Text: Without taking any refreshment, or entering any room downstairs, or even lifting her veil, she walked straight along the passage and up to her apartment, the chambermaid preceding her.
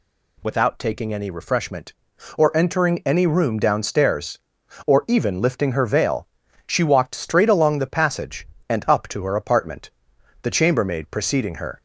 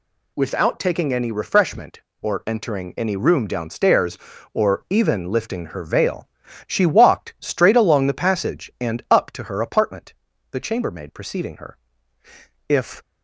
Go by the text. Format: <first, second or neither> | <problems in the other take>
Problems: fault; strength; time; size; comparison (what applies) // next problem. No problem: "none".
first | goes on to say "If"; slight; from 12.6 s on; 0.34 s long